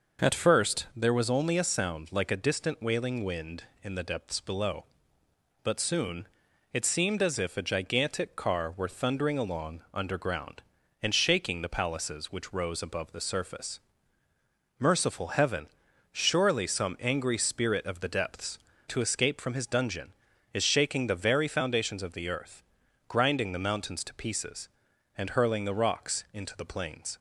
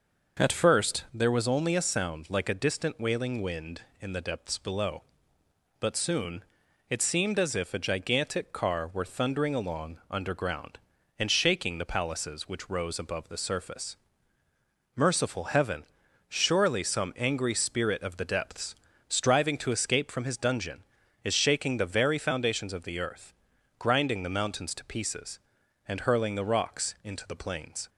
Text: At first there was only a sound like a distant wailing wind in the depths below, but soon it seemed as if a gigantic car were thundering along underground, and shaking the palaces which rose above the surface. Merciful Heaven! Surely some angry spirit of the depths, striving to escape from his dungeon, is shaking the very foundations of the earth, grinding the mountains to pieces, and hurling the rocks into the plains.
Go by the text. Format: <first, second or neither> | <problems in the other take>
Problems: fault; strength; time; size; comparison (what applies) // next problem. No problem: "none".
second | pauses between "soon" and "it"; noticeable; at 6.2 s; 0.46 s long; noticeable in the second // skips "striving"; at 18.7 s